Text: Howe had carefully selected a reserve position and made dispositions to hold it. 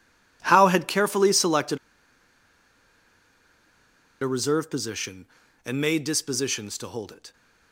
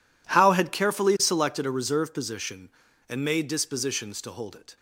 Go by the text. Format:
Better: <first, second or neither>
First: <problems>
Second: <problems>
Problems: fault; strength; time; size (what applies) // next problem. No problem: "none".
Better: second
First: pauses between "selected" and "a"; strong; at 1.7 s; 2.4 s long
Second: none